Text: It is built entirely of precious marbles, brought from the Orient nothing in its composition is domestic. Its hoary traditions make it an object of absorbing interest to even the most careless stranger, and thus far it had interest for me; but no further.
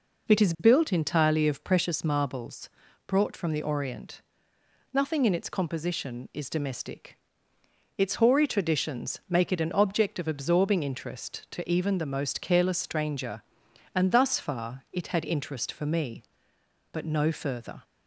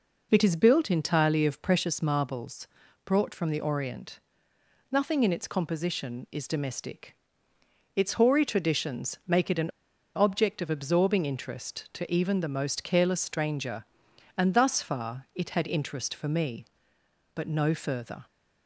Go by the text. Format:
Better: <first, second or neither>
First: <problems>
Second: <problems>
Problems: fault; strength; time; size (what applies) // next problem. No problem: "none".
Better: first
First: pauses between "Orient" and "nothing"; noticeable; at 4.2 s; 0.72 s long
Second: pauses between "Orient" and "nothing"; noticeable; at 4.1 s; 0.72 s long // pauses between "an" and "object"; noticeable; at 9.6 s; 0.46 s long